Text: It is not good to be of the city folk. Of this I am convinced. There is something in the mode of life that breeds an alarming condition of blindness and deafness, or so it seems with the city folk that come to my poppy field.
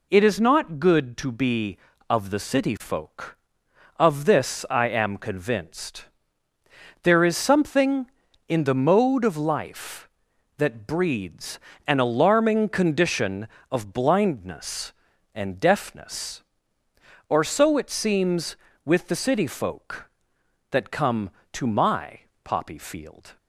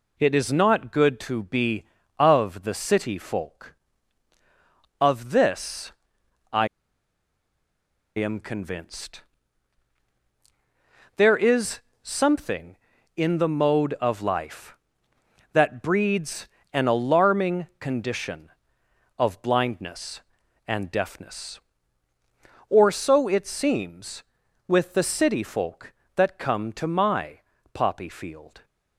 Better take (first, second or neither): first